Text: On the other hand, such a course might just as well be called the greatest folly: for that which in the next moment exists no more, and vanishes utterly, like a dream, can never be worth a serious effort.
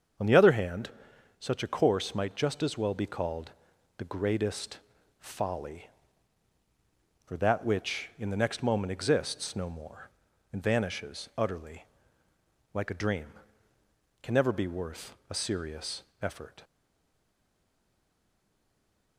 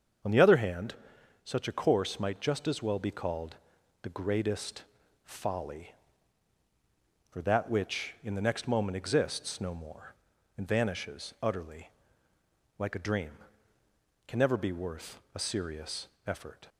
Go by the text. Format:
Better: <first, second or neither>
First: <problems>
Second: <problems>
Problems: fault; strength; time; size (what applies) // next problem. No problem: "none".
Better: second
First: starts louder than the rest; until 1.7 s; 7 dB // pauses between "called" and "the"; noticeable; at 3.5 s; 0.46 s long // pauses between "greatest" and "folly"; at 4.7 s; 0.40 s long // pauses between "serious" and "effort"; slight; at 16.0 s; 0.20 s long // stays silent after the last word; strong; from 16.6 s on; 2.5 s long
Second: starts louder than the rest; until 1.7 s; 7 dB // pauses between "called" and "the"; noticeable; at 3.5 s; 0.46 s long // pauses between "greatest" and "folly"; at 4.8 s; 0.40 s long // pauses between "serious" and "effort"; slight; at 16.0 s; 0.20 s long